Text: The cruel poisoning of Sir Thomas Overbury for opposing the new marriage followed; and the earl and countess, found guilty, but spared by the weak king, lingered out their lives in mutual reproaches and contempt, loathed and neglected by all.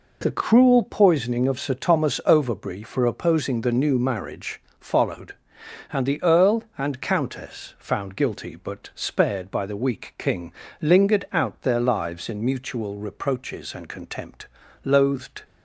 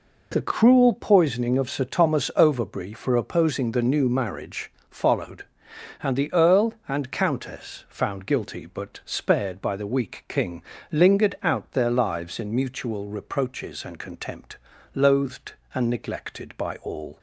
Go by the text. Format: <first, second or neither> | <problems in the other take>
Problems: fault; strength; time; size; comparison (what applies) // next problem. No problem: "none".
second | pauses between "marriage" and "followed"; slight; at 4.6 s; 0.18 s long; slight in the second // stops before "and neglected by all"; at 15.4 s